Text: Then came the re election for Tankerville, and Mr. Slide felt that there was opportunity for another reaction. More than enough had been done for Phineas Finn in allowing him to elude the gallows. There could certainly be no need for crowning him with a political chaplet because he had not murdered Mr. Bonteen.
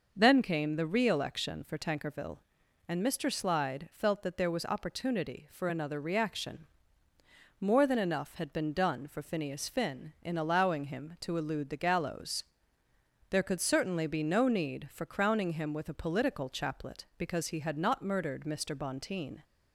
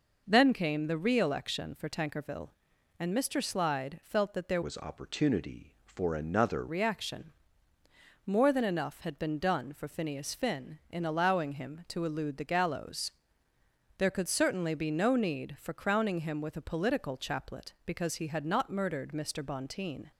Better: first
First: none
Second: changes voice from "was" to "another"; from 4.6 to 6.6 s; 2.0 s long

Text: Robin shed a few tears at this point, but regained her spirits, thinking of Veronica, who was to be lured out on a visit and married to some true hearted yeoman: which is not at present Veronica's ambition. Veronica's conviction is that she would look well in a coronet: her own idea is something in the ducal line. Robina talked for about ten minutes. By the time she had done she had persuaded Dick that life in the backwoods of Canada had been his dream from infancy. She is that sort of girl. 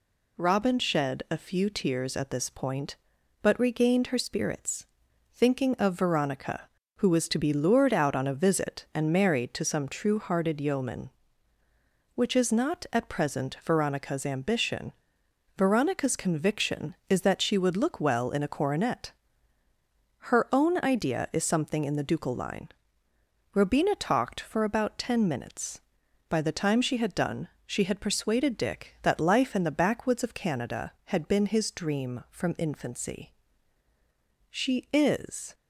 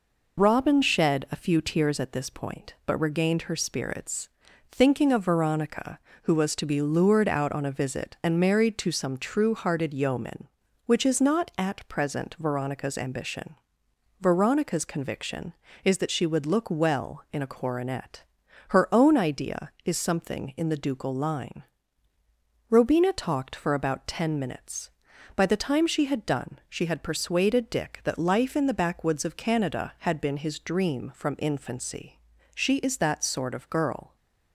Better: second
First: pauses between "done" and "she"; slight; at 27.4 s; 0.16 s long // stops before "that sort of girl"; at 35.5 s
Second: none

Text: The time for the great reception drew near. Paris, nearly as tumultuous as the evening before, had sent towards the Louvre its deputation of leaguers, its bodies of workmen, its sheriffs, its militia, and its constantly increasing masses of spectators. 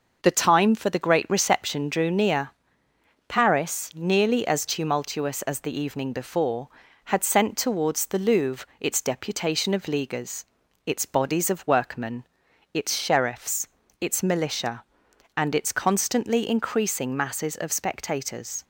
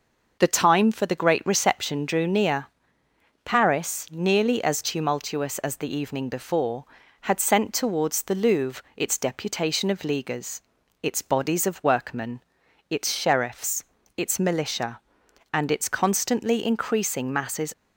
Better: first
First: none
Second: stops before "of spectators"; at 17.7 s

